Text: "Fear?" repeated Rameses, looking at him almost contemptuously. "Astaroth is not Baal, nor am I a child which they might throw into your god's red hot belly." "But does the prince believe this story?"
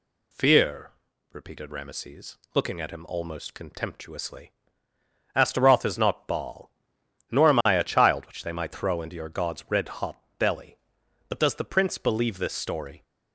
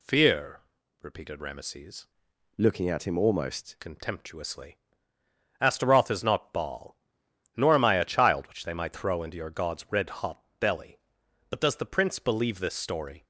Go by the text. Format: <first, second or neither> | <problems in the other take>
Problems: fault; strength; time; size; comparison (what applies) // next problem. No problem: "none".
first | changes voice from "looking" to "almost"; from 2.5 to 3.7 s; 1.2 s long // pauses between "hot" and "belly"; slight; at 10.4 s; 0.16 s long; slight in the first